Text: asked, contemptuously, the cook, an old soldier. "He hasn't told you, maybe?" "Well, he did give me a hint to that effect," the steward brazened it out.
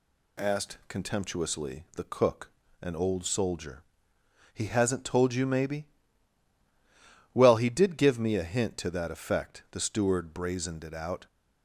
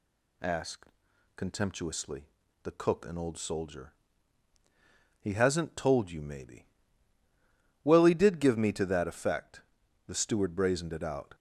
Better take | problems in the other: first | skips "a hint"; at 8.7 s

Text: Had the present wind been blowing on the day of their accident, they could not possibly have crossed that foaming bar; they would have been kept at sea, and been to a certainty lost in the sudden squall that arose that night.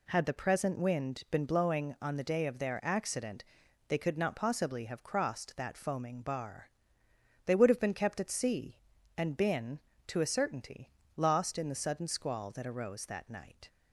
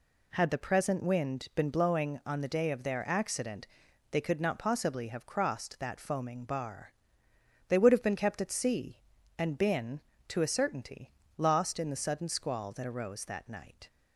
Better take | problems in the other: neither | pauses between "certainty" and "lost"; slight; the same in both

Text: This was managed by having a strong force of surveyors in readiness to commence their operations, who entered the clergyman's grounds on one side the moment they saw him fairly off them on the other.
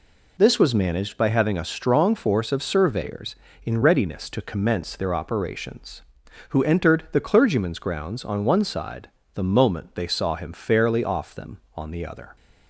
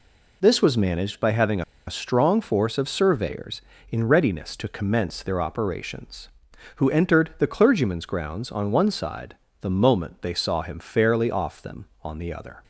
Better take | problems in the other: first | pauses between "having" and "a"; slight; at 1.6 s; 0.25 s long // pauses between "side" and "the"; slight; at 9.3 s; 0.24 s long; slight in the first

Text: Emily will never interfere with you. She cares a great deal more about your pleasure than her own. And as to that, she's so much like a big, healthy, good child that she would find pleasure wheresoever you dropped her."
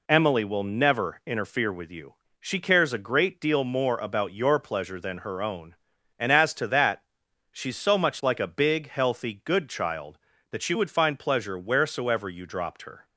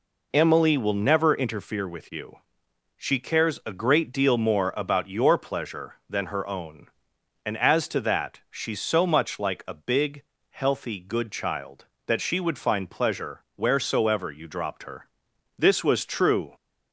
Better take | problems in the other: first | goes on to say "This was true"; noticeable; from 15.5 s on; 0.96 s long

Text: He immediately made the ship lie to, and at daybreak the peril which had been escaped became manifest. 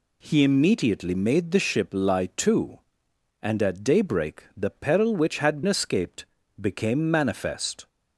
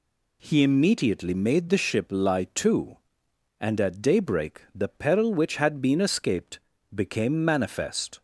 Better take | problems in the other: second | skips "been"; at 5.6 s // pauses between "escaped" and "became"; slight; at 6.2 s; 0.36 s long; slight in the second

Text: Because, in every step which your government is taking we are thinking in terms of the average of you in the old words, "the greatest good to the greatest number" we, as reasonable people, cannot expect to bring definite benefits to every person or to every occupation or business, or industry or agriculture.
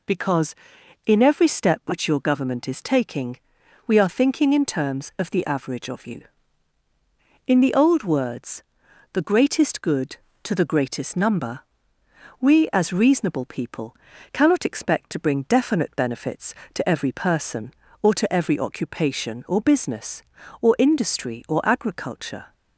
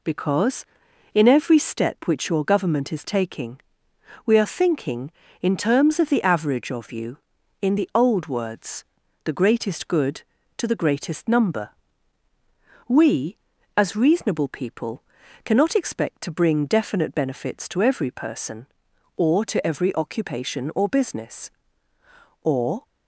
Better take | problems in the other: first | pauses between "taking" and "we"; noticeable; at 3.5 s; 0.66 s long; noticeable in the first // pauses between "number" and "we"; at 11.7 s; 1.1 s long; noticeable in the first // stops before "industry or agriculture"; at 22.8 s

